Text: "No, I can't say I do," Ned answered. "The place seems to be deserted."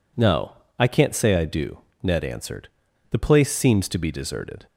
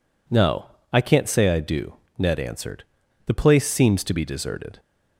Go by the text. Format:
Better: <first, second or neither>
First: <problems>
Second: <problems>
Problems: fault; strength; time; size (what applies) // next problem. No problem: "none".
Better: neither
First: none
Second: none